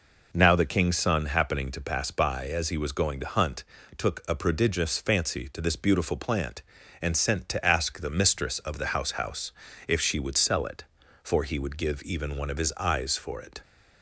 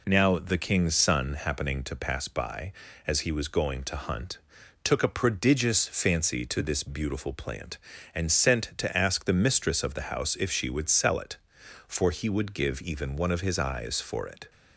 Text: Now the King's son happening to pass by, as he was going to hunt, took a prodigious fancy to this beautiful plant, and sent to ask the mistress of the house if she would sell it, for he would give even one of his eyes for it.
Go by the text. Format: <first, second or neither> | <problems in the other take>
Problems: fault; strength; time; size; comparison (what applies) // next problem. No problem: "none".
second | says "house" twice; at 9.1 s